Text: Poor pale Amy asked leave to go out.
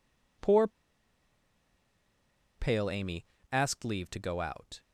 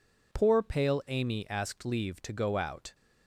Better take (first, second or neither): second